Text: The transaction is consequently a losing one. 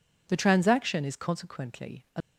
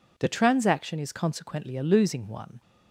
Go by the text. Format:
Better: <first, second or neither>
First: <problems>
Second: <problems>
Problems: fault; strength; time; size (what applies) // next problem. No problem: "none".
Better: second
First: stops before "losing one"; at 2.2 s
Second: none